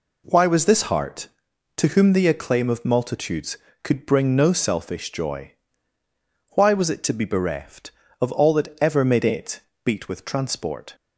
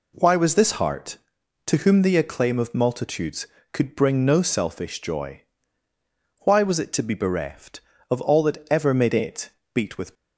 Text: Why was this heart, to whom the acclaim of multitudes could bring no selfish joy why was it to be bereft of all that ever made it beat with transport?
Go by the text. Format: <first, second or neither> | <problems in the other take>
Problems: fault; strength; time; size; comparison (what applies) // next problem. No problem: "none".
first | pauses between "joy" and "why"; at 5.4 s; 1.0 s long; also in the first // pauses between "it" and "beat"; slight; at 9.4 s; 0.24 s long; slight in the first // stops before "transport"; at 10.1 s